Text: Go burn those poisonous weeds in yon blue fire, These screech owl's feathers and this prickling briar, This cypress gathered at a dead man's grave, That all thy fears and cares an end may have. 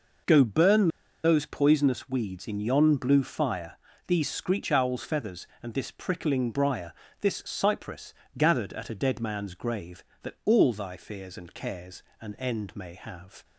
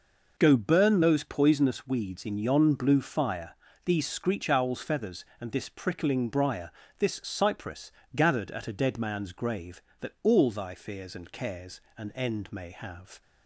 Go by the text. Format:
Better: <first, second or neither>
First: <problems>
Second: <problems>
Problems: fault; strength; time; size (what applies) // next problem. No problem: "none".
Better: second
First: pauses between "burn" and "those"; slight; at 0.8 s; 0.35 s long // pauses between "cypress" and "gathered"; slight; at 8.1 s; 0.24 s long // pauses between "cares" and "an"; slight; at 12.0 s; 0.18 s long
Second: pauses between "cypress" and "gathered"; slight; at 7.9 s; 0.24 s long // pauses between "cares" and "an"; slight; at 11.7 s; 0.16 s long